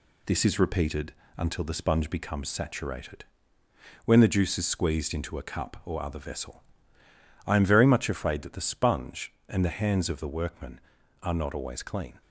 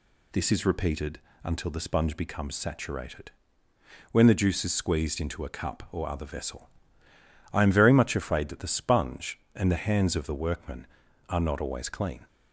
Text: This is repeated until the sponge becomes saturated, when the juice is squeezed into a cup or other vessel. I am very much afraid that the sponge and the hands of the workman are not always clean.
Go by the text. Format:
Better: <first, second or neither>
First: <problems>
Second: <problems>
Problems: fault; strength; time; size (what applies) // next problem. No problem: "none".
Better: second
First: gets quieter; throughout; 3.5 dB // pauses between "repeated" and "until"; slight; at 1.1 s; 0.24 s long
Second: pauses between "repeated" and "until"; slight; at 1.1 s; 0.24 s long